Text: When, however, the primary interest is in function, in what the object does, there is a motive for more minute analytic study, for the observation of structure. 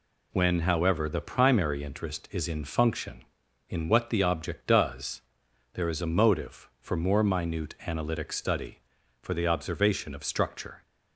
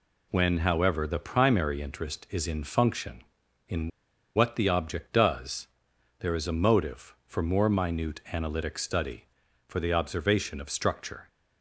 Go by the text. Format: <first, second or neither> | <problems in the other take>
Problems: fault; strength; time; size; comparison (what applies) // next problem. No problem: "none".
first | pauses between "in" and "what"; noticeable; at 3.8 s; 0.47 s long